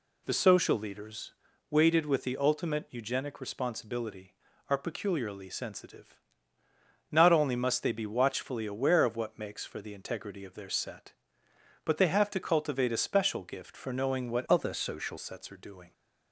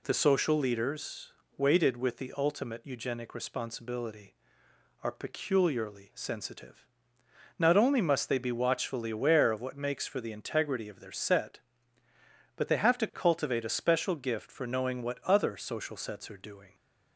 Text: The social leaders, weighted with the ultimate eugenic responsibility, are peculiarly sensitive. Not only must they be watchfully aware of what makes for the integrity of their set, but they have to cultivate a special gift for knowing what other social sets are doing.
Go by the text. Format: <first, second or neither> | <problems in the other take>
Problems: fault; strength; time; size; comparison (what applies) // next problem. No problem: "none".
second | changes voice from "other" to "social"; from 14.4 to 15.1 s; 0.7 s long